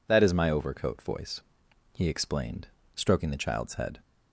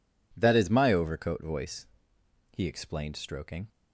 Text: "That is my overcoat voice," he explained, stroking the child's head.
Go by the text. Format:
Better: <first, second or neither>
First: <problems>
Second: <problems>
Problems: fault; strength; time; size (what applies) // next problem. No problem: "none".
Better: first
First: none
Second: stops before "the child's head"; at 3.6 s